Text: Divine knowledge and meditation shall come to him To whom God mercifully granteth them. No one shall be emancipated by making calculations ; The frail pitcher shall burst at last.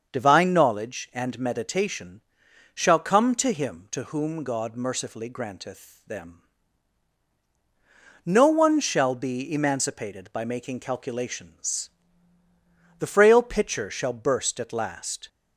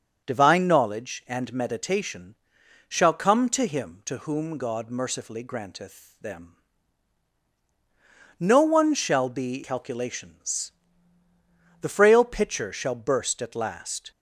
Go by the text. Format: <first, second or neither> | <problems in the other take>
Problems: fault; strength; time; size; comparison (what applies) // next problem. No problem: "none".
first | starts louder than the rest; until 1.2 s; 6.5 dB; also in the first // pauses between "meditation" and "shall"; noticeable; at 2.3 s; 0.52 s long; noticeable in the first // skips "emancipated by making"; at 9.6 s